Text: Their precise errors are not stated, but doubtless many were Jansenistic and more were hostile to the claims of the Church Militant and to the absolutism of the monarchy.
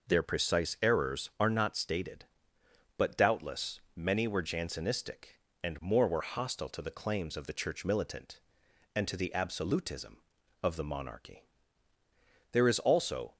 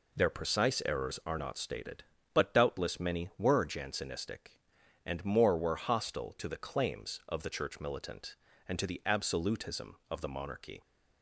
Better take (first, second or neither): second